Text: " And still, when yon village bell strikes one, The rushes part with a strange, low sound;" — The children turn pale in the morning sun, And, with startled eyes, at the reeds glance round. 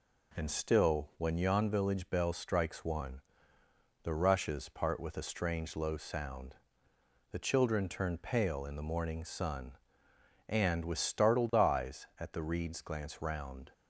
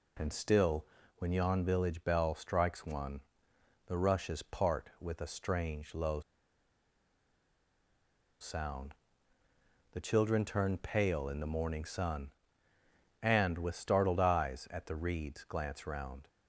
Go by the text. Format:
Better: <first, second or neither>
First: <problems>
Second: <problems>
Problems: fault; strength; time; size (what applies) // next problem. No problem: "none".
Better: first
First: none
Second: pauses between "low" and "sound"; strong; at 6.2 s; 2.1 s long